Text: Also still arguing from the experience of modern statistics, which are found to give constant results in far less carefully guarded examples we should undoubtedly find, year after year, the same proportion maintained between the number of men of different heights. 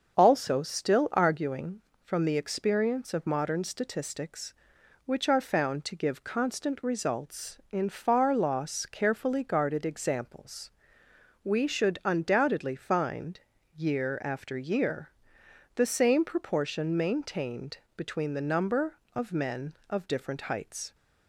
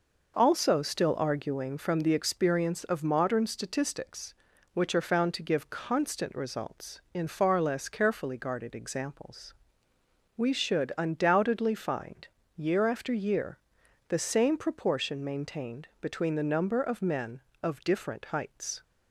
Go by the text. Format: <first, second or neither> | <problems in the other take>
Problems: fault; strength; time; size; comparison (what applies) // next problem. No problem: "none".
second | starts louder than the rest; until 1.2 s; 6.5 dB // says "loss" for "less"; at 8.3 s // pauses between "examples" and "we"; noticeable; at 10.7 s; 0.76 s long; noticeable in the second // pauses between "maintained" and "between"; slight; at 17.7 s; 0.20 s long